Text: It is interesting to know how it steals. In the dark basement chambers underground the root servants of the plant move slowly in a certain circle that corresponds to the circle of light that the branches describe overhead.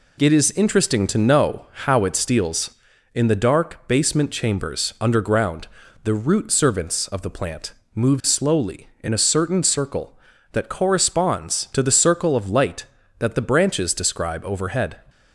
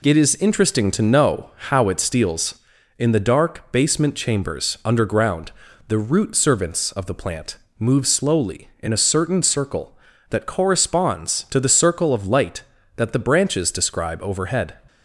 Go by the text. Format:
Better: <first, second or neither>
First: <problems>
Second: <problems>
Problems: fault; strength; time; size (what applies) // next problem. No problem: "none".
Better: neither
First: pauses between "underground" and "the"; slight; at 5.6 s; 0.36 s long // pauses between "plant" and "move"; slight; at 7.7 s; 0.24 s long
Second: pauses between "underground" and "the"; slight; at 5.5 s; 0.36 s long // pauses between "plant" and "move"; slight; at 7.5 s; 0.24 s long